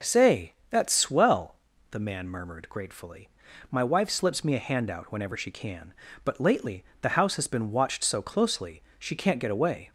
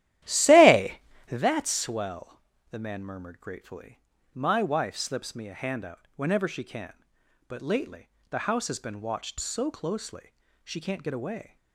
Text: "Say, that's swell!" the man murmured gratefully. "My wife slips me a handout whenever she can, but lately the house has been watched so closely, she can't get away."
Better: first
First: pauses between "lately" and "the"; slight; at 6.8 s; 0.18 s long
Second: starts louder than the rest; strong; until 1.4 s; 13 dB // pauses between "lately" and "the"; slight; at 8.0 s; 0.24 s long

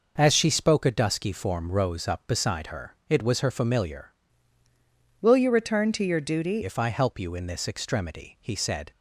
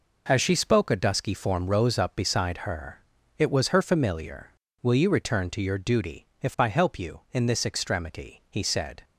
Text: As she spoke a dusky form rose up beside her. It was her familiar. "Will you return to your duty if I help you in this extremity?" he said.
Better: second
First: changes voice from "Will" to "duty"; from 5.2 to 6.6 s; 1.4 s long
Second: none

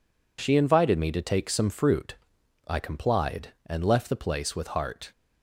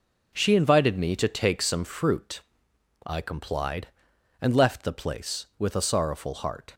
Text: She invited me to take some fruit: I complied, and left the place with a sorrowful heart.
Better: second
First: skips "a sorrowful"; at 4.6 s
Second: none

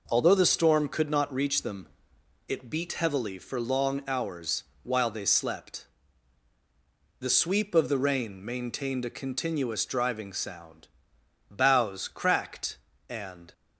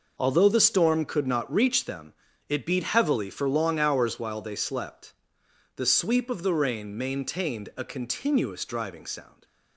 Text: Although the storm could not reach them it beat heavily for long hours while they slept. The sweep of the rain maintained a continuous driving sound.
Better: second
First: pauses between "them" and "it"; noticeable; at 1.8 s; 0.62 s long // pauses between "hours" and "while"; slight; at 4.6 s; 0.22 s long // goes on to say "Boughs cracked and"; strong; from 11.5 s on; 2.0 s long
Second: pauses between "them" and "it"; slight; at 2.1 s; 0.36 s long

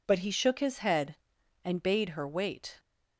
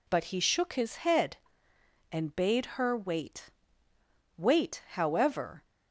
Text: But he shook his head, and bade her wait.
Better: first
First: none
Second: goes on to say "Wait however"; noticeable; from 4.3 s on; 1.2 s long

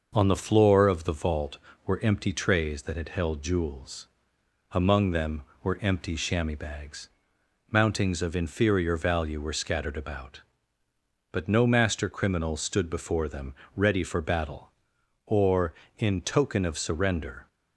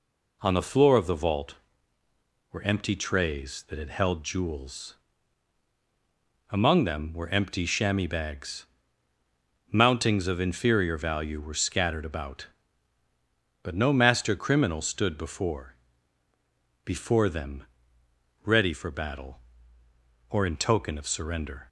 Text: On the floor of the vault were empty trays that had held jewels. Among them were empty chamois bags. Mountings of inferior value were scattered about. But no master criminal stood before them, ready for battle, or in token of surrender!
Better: first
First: none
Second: says "before" twice; at 16.8 s

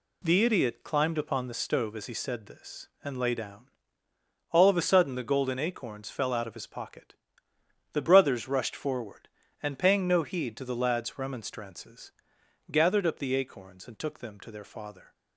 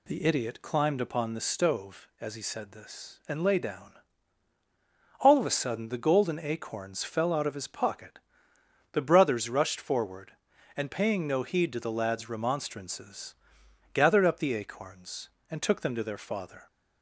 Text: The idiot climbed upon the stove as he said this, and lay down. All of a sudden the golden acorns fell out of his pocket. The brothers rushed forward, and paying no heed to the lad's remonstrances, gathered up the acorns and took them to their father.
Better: neither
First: none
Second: none

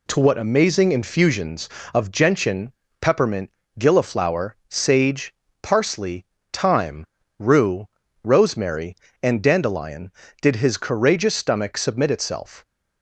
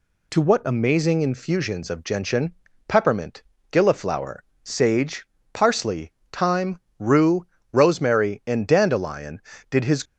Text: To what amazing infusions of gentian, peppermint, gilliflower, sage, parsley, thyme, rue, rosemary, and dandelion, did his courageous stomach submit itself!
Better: first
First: none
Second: stops before "courageous stomach submit itself"; at 10.0 s

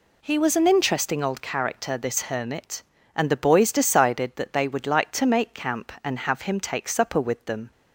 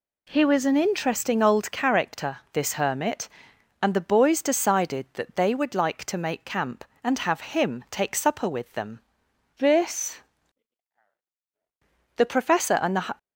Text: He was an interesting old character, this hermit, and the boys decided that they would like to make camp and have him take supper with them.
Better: first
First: none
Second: goes on to say "This the Professor and the"; strong; from 9.5 s on; 3.6 s long

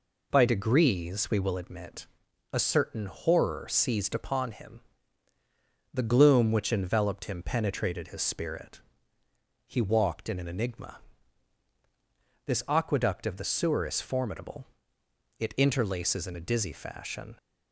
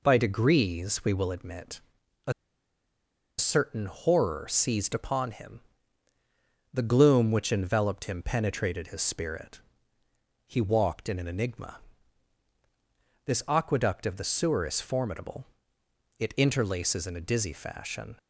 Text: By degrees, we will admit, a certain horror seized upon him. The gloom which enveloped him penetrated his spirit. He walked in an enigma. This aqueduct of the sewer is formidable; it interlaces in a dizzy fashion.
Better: first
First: none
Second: pauses between "a" and "certain"; at 2.3 s; 1.0 s long

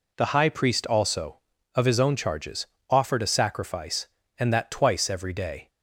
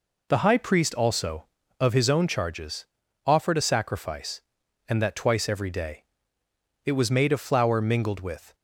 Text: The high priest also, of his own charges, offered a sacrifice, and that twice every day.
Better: first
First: none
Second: goes on to say "It was made of flour mingled with"; strong; from 6.8 s on; 1.7 s long

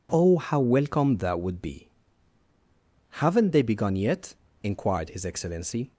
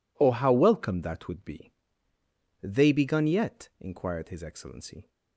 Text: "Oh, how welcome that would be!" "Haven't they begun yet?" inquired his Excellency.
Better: first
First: none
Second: skips "Haven't"; at 2.1 s

